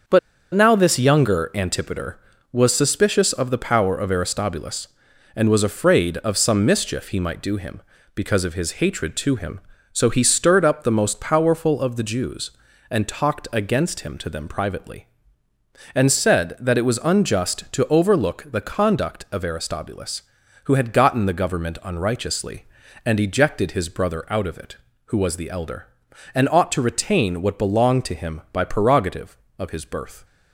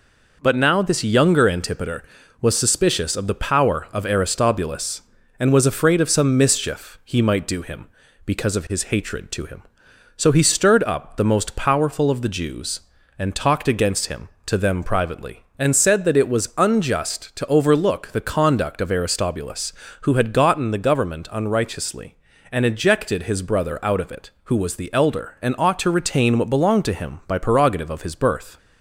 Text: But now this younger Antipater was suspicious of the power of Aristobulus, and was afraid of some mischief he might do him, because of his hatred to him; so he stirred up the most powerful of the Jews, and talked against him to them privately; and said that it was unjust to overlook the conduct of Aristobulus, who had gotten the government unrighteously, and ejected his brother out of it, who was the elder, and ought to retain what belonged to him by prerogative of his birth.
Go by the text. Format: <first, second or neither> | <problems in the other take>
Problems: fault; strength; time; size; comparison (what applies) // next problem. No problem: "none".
second | starts louder than the rest; until 1.4 s; 7 dB // pauses between "But" and "now"; slight; at 0.1 s; 0.35 s long